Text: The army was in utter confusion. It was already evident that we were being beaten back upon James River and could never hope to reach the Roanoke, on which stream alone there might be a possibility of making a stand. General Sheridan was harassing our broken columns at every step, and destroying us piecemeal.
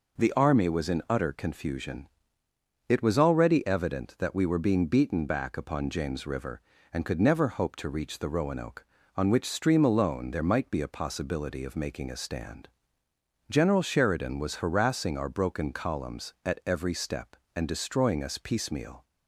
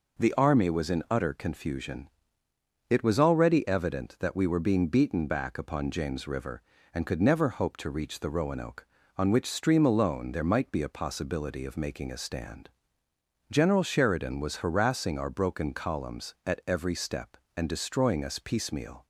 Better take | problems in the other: neither | none

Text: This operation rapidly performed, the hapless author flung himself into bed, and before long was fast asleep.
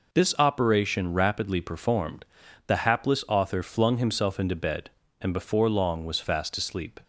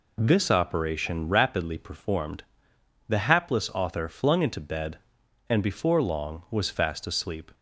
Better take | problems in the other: first | skips "himself"; at 4.4 s

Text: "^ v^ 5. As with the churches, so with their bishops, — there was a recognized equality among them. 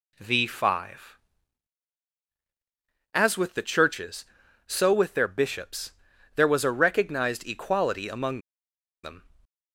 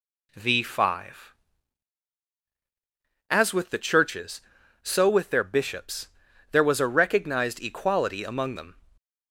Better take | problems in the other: second | pauses between "among" and "them"; noticeable; at 8.4 s; 0.63 s long

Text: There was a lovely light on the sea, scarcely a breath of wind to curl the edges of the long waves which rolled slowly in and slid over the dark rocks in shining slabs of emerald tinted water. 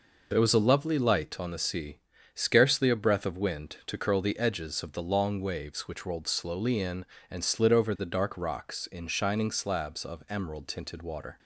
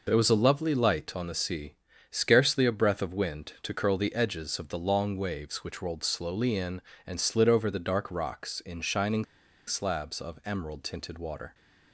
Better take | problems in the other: first | pauses between "shining" and "slabs"; at 9.2 s; 0.43 s long

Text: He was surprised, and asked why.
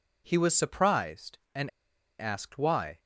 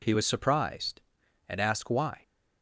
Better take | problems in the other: second | pauses between "and" and "asked"; noticeable; at 1.6 s; 0.50 s long

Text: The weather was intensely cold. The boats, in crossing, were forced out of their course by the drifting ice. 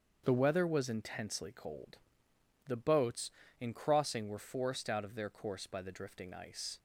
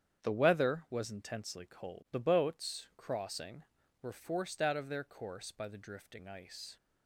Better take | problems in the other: first | starts louder than the rest; strong; until 1.2 s; 8.5 dB; also in the first // skips "in"; at 2.9 s

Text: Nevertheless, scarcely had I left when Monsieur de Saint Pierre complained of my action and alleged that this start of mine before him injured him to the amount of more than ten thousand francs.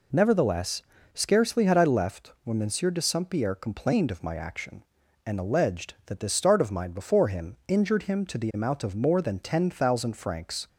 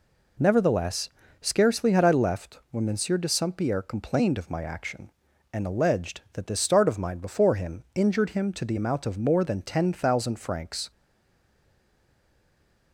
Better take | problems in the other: first | stays silent after the last word; noticeable; from 10.9 s on; 2.0 s long

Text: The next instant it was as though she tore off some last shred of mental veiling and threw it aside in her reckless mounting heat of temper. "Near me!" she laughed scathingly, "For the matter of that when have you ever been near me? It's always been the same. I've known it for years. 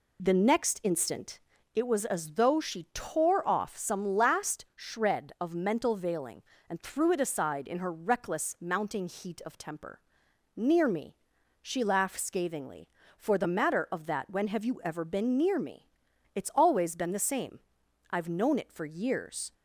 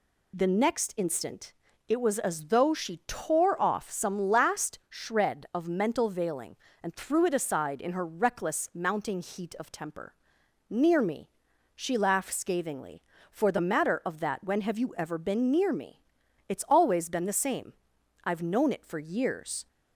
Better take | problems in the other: second | starts louder than the rest; slight; until 1.6 s; 2.5 dB // pauses between "instant" and "it"; slight; at 1.3 s; 0.34 s long; slight in the second

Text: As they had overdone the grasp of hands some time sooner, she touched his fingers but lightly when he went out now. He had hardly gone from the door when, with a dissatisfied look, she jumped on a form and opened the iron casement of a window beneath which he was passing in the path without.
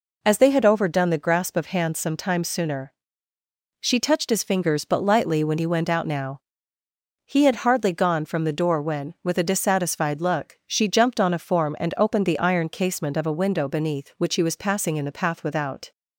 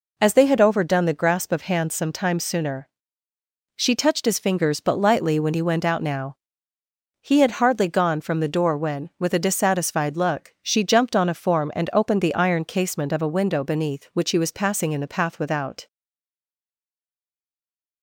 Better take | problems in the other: first | stays silent after the last word; from 15.8 s on; 2.2 s long

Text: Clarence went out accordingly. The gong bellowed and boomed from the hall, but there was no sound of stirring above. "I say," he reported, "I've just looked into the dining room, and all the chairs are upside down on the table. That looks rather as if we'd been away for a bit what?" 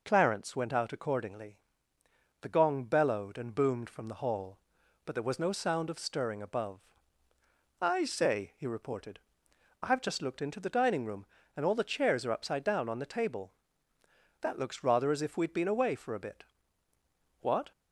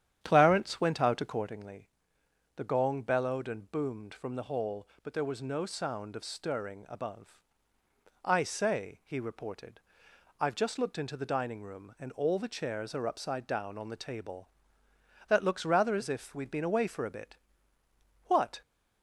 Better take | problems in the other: first | starts louder than the rest; strong; until 1.5 s; 10 dB // pauses between "bit" and "what"; noticeable; at 17.3 s; 0.88 s long; noticeable in the first

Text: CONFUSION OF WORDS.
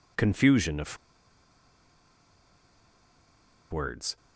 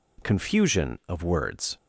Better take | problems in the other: second | pauses between "OF" and "WORDS"; strong; at 0.9 s; 2.7 s long

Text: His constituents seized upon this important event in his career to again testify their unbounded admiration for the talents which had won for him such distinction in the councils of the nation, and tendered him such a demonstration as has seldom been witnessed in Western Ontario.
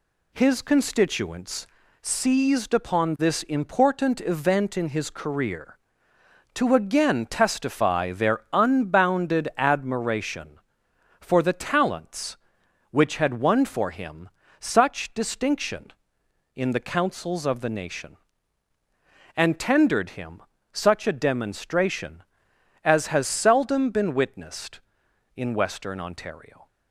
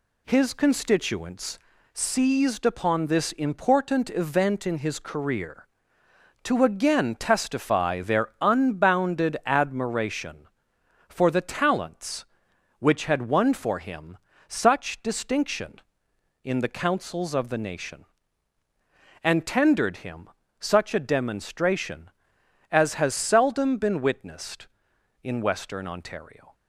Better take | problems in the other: neither | pauses between "constituents" and "seized"; slight; the same in both // pauses between "him" and "such"; slight; the same in both // pauses between "him" and "such"; slight; the same in both

